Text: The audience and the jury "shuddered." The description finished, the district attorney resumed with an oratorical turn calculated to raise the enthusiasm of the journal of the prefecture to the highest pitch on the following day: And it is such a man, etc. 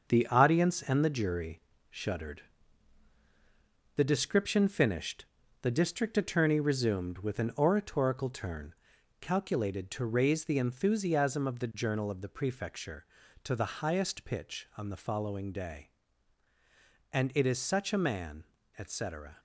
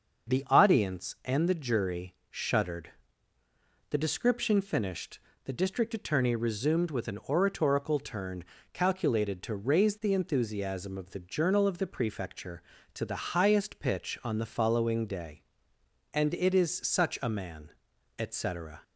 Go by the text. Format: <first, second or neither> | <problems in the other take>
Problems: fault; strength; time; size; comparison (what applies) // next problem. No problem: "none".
second | gets quieter; noticeable; throughout; 6 dB // starts louder than the rest; until 1.0 s; 6.5 dB; also in the second // pauses between "jury" and "shuddered"; slight; at 1.6 s; 0.28 s long; slight in the second // pauses between "turn" and "calculated"; noticeable; at 8.7 s; 0.46 s long; slight in the second